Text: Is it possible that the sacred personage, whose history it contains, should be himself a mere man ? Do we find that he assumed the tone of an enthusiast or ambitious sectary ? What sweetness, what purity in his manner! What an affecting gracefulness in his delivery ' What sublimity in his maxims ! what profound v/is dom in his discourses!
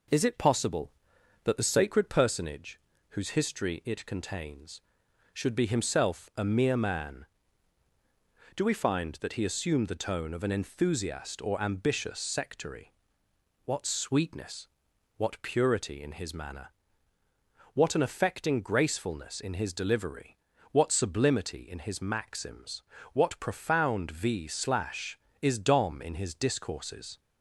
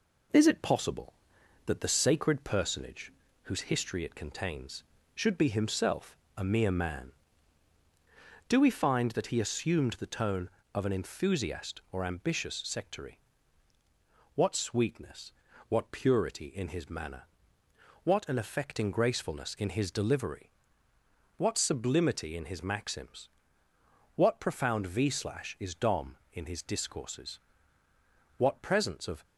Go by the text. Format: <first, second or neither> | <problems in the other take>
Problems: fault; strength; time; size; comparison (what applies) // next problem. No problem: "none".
first | pauses between "himself" and "a"; slight; at 6.1 s; 0.22 s long // goes on to say "What presence of"; noticeable; from 28.3 s on; 0.86 s long